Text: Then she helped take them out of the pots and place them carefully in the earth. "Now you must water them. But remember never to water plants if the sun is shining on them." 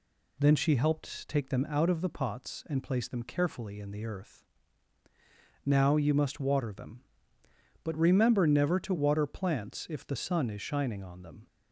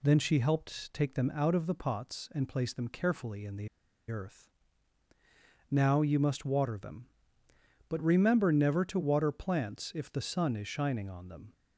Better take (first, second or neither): first